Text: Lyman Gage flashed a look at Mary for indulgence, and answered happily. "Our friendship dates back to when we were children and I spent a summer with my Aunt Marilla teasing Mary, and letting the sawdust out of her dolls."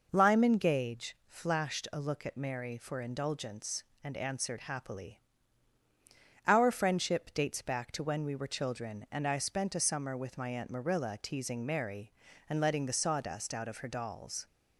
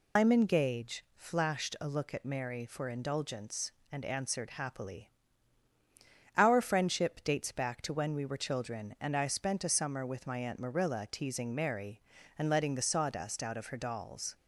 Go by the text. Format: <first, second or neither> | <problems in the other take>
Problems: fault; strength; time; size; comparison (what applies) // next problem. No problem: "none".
first | loses the start of "Lyman"; at 0.1 s; 180 ms